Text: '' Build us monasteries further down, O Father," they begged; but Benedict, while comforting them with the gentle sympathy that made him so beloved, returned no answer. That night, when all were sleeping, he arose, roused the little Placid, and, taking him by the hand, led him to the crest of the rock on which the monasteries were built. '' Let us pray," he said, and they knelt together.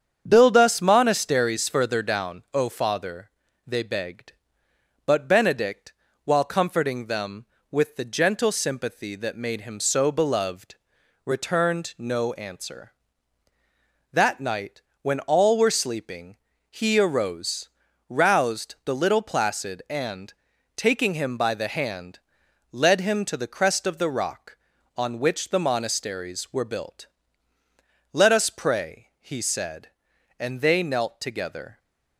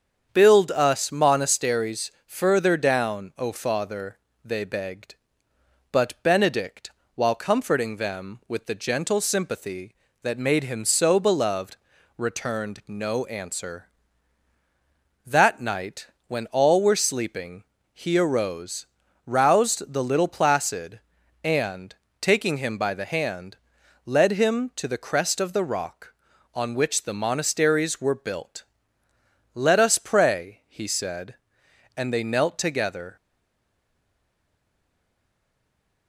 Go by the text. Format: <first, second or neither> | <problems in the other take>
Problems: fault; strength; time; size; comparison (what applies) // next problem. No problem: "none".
first | starts louder than the rest; strong; until 1.3 s; 7.5 dB; strong in the first // stays silent after the last word; strong; from 33.1 s on; 2.9 s long